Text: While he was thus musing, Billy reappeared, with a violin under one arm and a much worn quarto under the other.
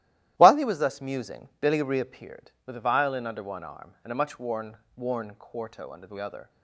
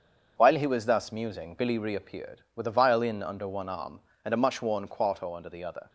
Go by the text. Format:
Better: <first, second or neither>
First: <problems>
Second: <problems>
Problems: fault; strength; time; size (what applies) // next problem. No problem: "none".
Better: second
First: starts louder than the rest; strong; until 1.3 s; 13.5 dB // says "worn" twice; at 4.9 s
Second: starts louder than the rest; until 1.3 s; 7 dB